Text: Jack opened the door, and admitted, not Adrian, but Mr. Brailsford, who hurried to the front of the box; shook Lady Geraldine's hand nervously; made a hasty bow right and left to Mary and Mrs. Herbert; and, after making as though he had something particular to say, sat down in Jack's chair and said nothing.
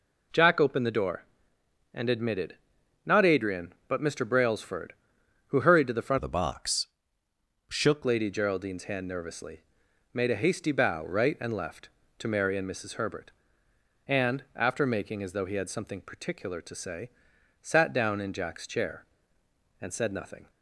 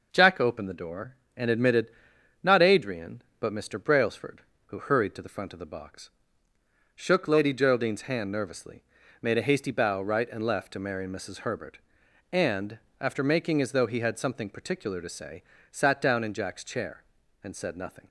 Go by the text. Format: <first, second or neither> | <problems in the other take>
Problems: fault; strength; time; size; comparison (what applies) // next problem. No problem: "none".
second | changes voice from "of" to "shook"; from 6.1 to 8.0 s; 1.9 s long